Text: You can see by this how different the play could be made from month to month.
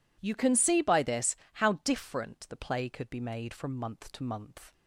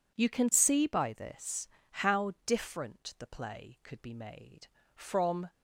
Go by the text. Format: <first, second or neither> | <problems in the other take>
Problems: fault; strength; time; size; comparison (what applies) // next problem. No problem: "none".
first | pauses between "this" and "how"; slight; at 1.6 s; 0.24 s long; slight in the first // stops before "month to month"; at 5.4 s